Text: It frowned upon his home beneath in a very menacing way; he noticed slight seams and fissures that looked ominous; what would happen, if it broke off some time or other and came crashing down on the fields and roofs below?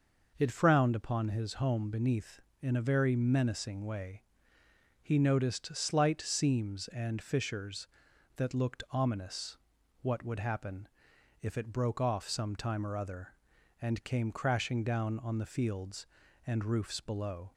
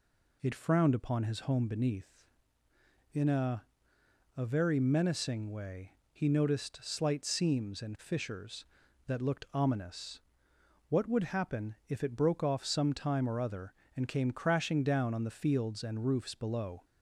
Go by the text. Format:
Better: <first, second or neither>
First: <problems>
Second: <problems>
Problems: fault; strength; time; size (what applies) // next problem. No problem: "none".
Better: first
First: none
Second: says "a" twice; at 4.3 s